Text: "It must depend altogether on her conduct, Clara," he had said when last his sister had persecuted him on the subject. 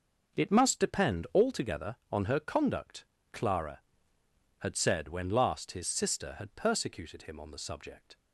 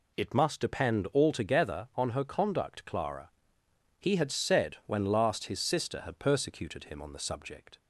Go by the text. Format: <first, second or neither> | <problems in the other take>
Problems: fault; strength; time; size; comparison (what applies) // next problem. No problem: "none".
second | starts louder than the rest; noticeable; until 1.4 s; 6 dB // skips "he"; at 4.2 s